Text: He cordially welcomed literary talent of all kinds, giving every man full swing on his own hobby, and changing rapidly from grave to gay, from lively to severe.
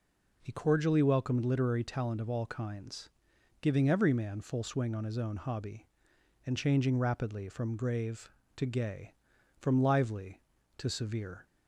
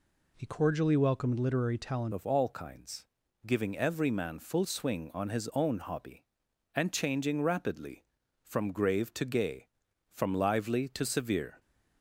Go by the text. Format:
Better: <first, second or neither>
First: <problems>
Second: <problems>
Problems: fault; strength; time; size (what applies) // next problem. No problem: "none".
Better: first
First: none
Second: changes voice at "of"; from 2.1 s on; 9.4 s long